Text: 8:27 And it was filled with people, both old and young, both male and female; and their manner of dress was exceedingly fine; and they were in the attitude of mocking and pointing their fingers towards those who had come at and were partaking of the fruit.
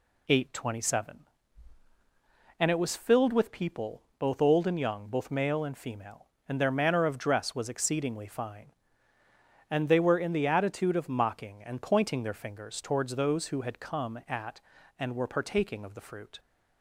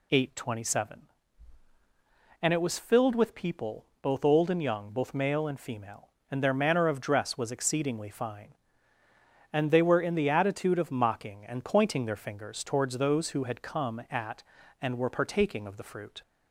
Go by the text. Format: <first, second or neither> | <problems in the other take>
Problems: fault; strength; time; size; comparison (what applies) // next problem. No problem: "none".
second | gets quieter; slight; throughout; 3 dB